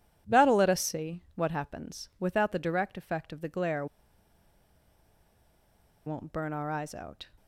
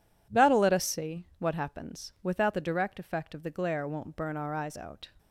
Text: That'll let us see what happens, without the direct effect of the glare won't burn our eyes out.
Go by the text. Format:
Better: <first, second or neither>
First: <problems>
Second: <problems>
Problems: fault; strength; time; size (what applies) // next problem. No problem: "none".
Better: second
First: pauses between "glare" and "won't"; strong; at 3.8 s; 2.2 s long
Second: none